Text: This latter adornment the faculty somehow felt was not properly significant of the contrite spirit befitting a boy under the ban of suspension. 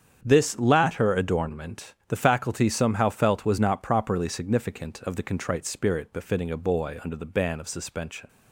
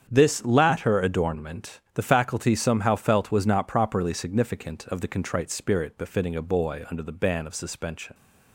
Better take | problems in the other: neither | starts louder than the rest; strong; the same in both

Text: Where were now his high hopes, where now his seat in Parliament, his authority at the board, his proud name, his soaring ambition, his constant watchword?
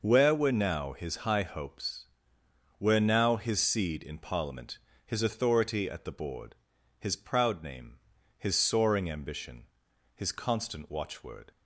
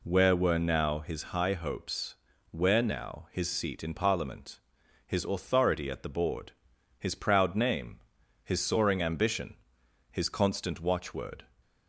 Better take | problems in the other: second | says "seed" for "seat"; at 3.6 s

